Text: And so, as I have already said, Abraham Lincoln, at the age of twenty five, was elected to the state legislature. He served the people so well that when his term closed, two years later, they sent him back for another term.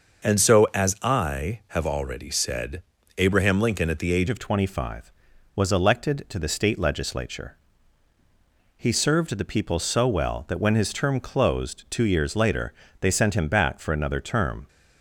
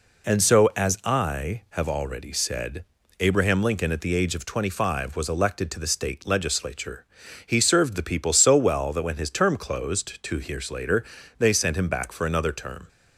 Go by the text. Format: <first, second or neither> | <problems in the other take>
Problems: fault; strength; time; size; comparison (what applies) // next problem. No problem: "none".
second | starts louder than the rest; noticeable; until 1.3 s; 6 dB // changes voice at "of"; from 4.2 s on; 10.4 s long